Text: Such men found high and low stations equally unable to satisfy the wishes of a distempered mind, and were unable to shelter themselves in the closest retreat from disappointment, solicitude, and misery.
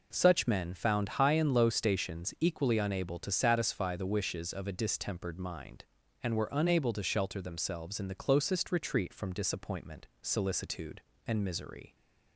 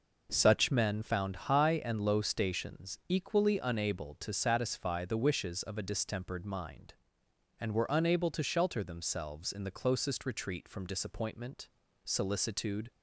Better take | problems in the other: first | stops before "and misery"; at 12.9 s

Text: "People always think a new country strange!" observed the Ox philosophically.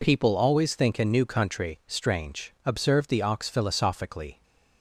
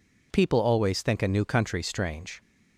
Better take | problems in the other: first | stops before "observed the Ox philosophically"; at 2.3 s

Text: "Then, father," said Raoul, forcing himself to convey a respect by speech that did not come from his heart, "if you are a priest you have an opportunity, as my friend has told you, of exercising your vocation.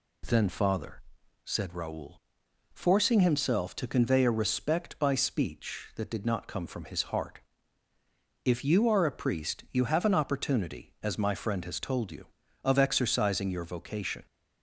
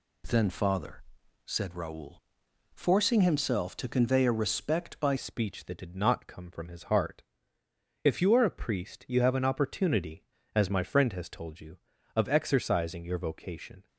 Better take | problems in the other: first | changes voice at "speech"; from 5.1 s on; 8.7 s long

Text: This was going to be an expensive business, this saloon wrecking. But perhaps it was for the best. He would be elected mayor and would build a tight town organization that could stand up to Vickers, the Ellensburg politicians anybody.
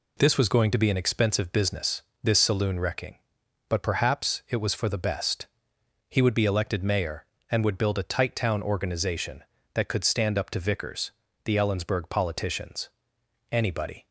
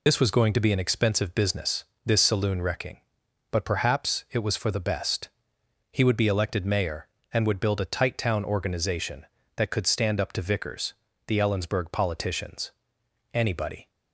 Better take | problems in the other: first | loses the start of "This"; at 0.0 s; 60 ms // pauses between "politicians" and "anybody"; noticeable; at 12.7 s; 0.60 s long; noticeable in the first

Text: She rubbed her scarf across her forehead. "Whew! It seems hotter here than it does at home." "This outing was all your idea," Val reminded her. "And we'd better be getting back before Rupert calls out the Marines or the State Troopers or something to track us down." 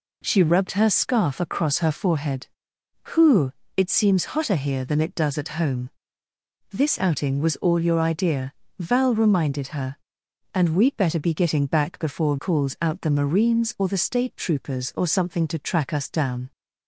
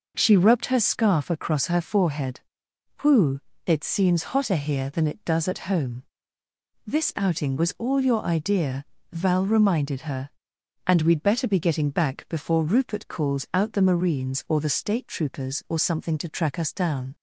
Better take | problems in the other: second | skips "Rupert"; at 12.3 s

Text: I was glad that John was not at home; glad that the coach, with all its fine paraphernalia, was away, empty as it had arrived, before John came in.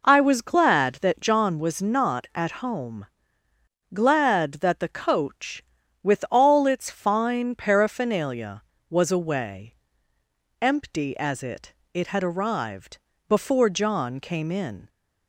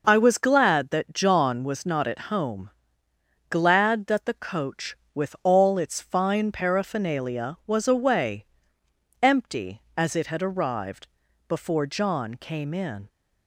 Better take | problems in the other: second | says "it" twice; at 11.9 s

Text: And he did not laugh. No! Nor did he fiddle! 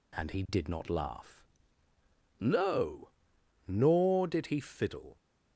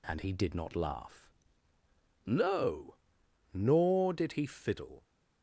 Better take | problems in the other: neither | none

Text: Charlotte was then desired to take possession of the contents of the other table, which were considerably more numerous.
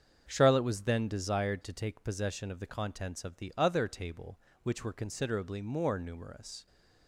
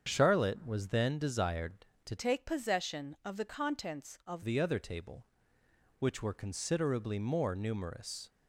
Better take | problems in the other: first | starts louder than the rest; strong; until 1.0 s; 7.5 dB; also in the first // changes voice from "take" to "of"; from 2.1 to 4.4 s; 2.3 s long

